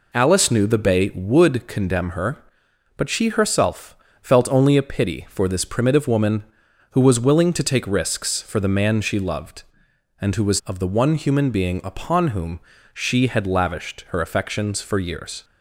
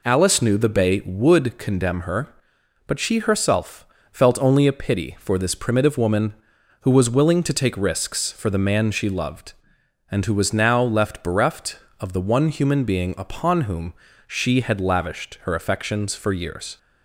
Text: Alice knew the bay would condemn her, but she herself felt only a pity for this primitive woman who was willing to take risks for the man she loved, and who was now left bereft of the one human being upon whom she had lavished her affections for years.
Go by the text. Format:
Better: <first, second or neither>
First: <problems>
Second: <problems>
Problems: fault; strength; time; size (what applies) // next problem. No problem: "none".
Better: second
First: pauses between "herself" and "felt"; slight; at 3.9 s; 0.26 s long // skips "now left bereft"; at 10.6 s // pauses between "whom" and "she"; slight; at 12.6 s; 0.32 s long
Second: pauses between "herself" and "felt"; slight; at 3.8 s; 0.26 s long // pauses between "whom" and "she"; slight; at 13.9 s; 0.32 s long